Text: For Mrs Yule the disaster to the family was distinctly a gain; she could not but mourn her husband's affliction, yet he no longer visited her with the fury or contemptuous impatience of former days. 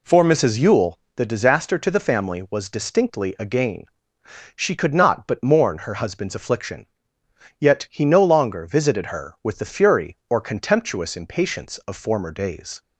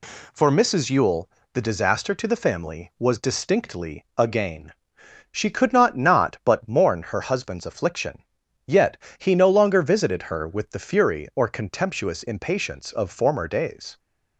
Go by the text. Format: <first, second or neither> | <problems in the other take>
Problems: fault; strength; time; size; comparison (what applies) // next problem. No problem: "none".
first | pauses between "Yule" and "the"; slight; at 1.2 s; 0.22 s long; slight in the first // says "not" twice; at 5.9 s // pauses between "yet" and "he"; slight; at 8.9 s; 0.22 s long